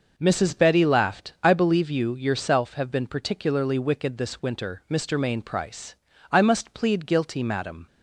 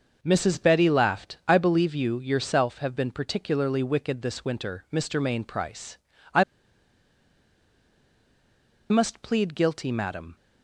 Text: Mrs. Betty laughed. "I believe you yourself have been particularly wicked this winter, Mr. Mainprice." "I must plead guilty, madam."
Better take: first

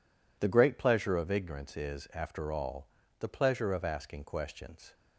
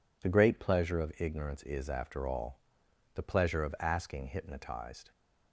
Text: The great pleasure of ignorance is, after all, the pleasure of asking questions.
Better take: first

